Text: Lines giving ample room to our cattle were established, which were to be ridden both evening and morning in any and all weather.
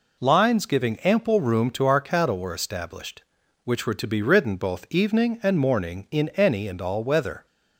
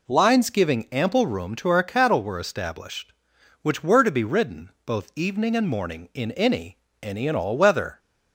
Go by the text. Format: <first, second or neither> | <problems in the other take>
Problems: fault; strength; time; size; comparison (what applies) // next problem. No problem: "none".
first | pauses between "ridden" and "both"; slight; at 4.6 s; 0.16 s long // says "any" twice; at 7.0 s